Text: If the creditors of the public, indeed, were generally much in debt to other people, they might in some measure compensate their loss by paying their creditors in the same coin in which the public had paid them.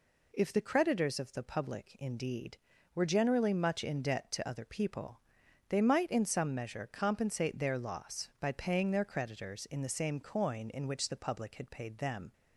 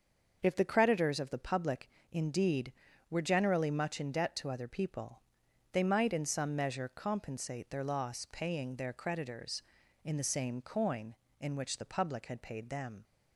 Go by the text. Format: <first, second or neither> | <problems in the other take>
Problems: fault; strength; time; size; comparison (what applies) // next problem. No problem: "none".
first | starts louder than the rest; until 1.4 s; 6.5 dB // skips "by"; at 8.2 s